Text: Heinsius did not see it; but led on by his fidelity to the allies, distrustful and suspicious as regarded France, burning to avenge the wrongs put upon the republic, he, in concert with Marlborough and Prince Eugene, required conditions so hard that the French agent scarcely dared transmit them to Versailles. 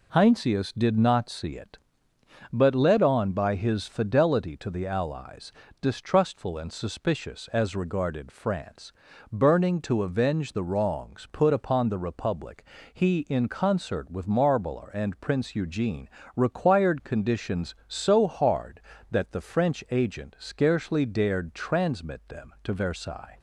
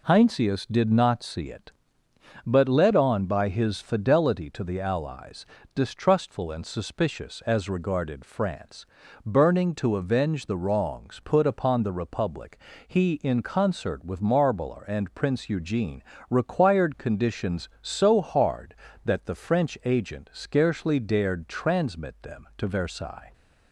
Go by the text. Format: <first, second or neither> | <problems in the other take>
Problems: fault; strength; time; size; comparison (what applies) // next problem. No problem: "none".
neither | none